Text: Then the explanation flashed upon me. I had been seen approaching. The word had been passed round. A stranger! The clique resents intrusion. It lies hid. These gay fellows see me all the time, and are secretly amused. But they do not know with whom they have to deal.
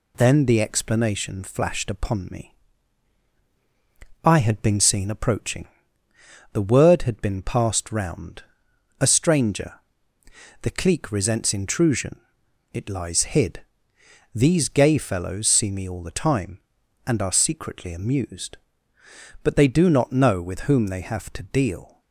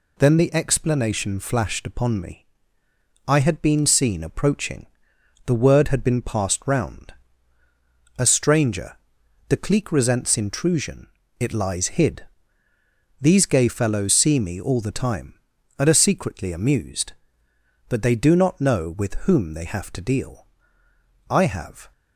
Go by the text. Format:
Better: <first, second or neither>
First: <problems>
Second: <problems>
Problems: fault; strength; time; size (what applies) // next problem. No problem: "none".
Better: first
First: none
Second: goes on to say "I have"; noticeable; from 21.2 s on; 0.62 s long